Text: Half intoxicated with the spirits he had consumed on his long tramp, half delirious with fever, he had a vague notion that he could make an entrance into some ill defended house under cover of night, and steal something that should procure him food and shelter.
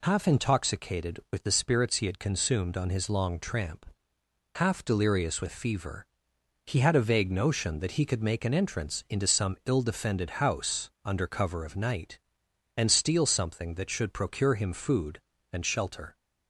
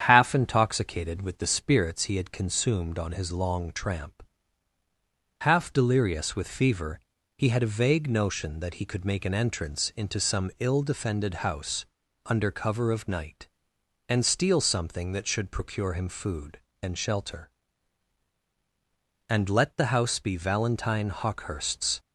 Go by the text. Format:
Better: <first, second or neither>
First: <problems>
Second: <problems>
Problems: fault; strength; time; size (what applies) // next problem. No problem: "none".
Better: first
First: none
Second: starts louder than the rest; strong; until 1.0 s; 8.5 dB // pauses between "house" and "under"; at 11.8 s; 0.40 s long // goes on to say "And let the house be Valentine Hawkehurst's"; strong; from 19.2 s on; 2.7 s long